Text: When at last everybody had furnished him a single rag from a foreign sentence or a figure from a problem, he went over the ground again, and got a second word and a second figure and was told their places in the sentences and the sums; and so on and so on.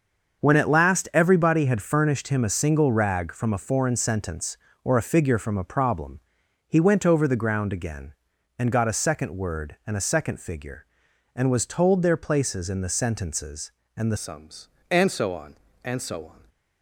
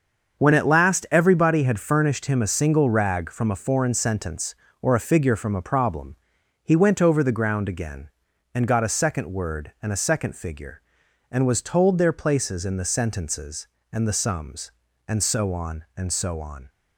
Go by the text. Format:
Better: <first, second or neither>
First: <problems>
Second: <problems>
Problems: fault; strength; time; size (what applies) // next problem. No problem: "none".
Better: second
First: starts louder than the rest; until 1.4 s; 6.5 dB // changes voice at "sums"; from 14.1 s on; 2.3 s long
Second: starts louder than the rest; until 1.4 s; 7 dB